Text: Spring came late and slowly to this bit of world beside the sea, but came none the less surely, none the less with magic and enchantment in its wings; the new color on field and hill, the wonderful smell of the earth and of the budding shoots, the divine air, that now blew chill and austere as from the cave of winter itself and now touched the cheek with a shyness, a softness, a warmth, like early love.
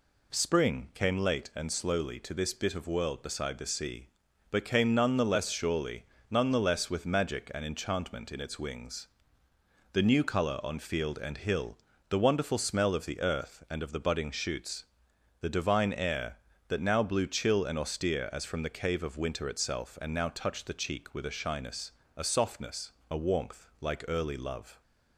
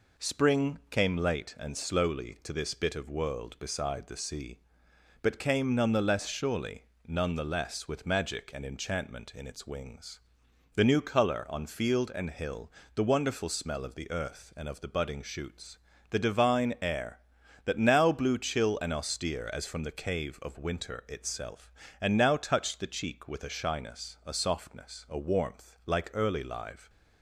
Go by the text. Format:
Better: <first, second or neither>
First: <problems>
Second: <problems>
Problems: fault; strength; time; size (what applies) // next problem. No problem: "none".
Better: first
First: none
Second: says "live" for "love"; at 26.4 s